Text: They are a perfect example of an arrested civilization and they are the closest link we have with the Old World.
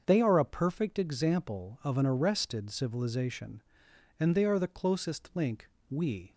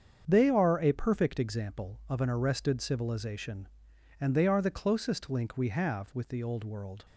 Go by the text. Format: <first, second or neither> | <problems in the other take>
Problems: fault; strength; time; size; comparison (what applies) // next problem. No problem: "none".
second | starts louder than the rest; until 1.0 s; 7 dB; strong in the second // pauses between "link" and "we"; slight; at 5.6 s; 0.20 s long // stops before "have with the Old World"; at 6.3 s